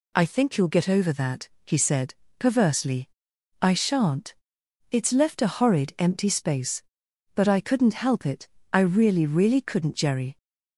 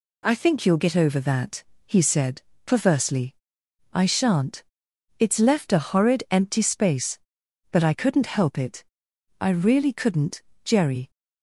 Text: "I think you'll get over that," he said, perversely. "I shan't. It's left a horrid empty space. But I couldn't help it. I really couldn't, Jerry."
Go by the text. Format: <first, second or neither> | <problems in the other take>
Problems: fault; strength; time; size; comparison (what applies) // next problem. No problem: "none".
second | says "really" twice; at 9.2 s